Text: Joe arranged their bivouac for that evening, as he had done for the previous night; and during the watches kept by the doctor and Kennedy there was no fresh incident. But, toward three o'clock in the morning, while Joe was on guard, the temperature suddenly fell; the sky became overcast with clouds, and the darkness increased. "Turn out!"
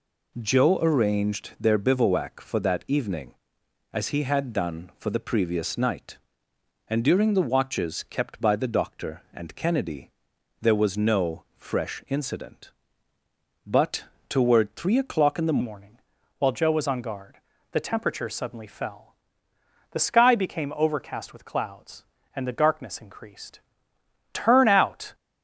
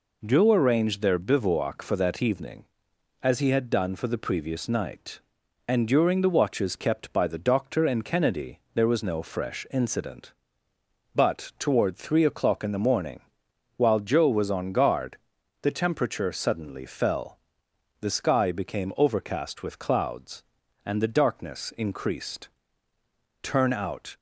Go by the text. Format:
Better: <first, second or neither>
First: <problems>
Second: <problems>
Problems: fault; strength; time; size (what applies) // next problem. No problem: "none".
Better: second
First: pauses between "Kennedy" and "there"; noticeable; at 10.1 s; 0.50 s long // changes voice at "morning"; from 15.6 s on; 9.5 s long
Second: pauses between "Kennedy" and "there"; slight; at 8.5 s; 0.16 s long